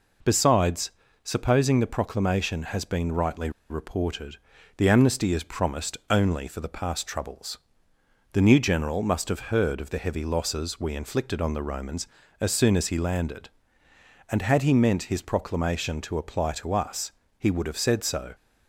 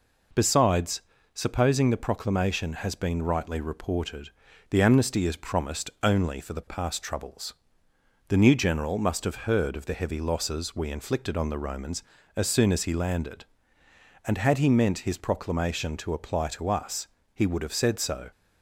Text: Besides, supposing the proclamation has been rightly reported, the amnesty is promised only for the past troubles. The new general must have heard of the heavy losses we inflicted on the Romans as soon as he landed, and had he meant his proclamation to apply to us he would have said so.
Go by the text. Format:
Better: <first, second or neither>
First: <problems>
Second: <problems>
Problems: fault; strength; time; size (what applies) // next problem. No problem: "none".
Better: second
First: pauses between "rightly" and "reported"; slight; at 3.4 s; 0.20 s long // pauses between "us" and "he"; slight; at 17.1 s; 0.26 s long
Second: pauses between "us" and "he"; slight; at 17.0 s; 0.26 s long